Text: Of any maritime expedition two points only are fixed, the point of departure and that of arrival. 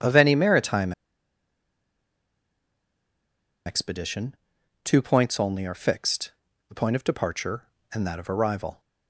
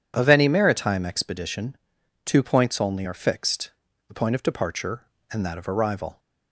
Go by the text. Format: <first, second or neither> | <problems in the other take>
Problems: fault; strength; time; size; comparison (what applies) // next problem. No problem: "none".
second | pauses between "maritime" and "expedition"; strong; at 0.9 s; 2.7 s long // pauses between "expedition" and "two"; noticeable; at 4.3 s; 0.48 s long; noticeable in the second